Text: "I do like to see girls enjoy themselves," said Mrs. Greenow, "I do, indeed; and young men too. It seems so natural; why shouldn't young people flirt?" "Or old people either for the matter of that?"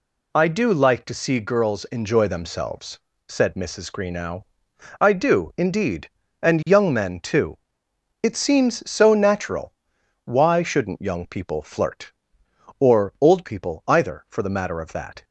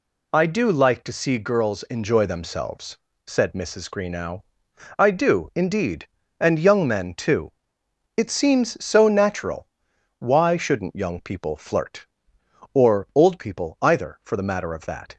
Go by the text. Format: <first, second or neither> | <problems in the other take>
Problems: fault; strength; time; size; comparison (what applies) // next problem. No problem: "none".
neither | none